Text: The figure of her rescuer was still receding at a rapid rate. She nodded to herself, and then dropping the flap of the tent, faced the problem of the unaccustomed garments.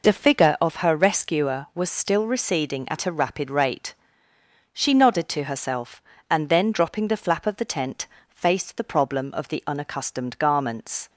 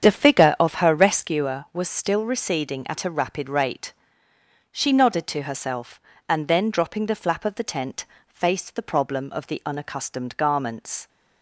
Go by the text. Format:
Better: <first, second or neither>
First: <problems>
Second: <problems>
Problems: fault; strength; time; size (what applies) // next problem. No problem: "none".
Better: first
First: none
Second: starts louder than the rest; strong; until 1.3 s; 8 dB